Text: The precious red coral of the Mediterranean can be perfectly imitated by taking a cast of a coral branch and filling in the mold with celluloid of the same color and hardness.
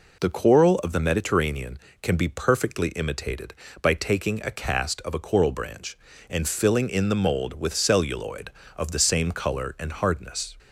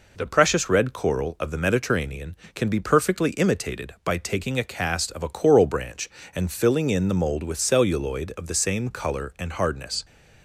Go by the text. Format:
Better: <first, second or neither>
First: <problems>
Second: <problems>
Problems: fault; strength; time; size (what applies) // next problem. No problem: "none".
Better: second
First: skips "precious red"; at 0.3 s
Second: none